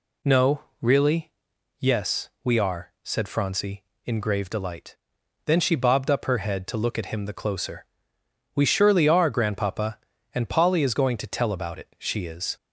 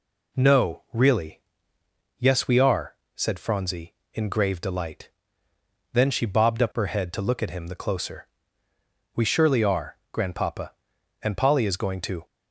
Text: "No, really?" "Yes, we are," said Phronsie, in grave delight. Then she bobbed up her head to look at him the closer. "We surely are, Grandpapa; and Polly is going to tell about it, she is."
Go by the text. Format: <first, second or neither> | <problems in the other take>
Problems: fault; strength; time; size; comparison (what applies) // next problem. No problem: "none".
first | stops before "tell about it she is"; at 12.2 s